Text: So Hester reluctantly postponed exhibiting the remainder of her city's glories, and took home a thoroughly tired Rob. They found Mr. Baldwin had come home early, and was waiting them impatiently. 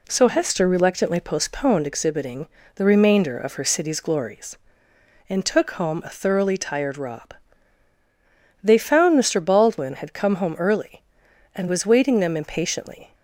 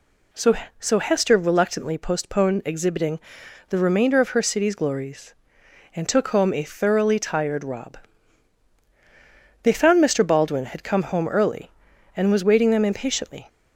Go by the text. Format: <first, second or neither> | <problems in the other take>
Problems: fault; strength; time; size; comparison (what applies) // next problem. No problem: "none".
first | says "So" twice; at 0.7 s // pauses between "exhibiting" and "the"; noticeable; at 3.1 s; 0.50 s long; slight in the first